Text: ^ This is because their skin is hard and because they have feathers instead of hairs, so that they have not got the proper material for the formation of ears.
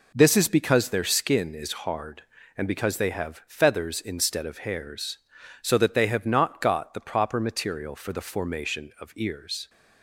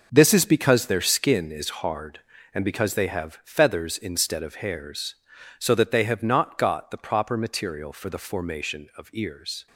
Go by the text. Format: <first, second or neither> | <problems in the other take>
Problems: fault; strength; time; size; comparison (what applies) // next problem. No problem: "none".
first | gets quieter; strong; throughout; 10.5 dB